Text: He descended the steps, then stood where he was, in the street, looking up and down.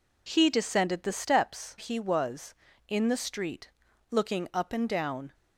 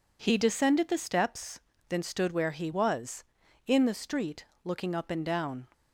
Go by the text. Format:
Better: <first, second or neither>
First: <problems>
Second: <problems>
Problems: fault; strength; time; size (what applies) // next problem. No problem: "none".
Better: second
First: skips "then stood where"; at 1.7 s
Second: none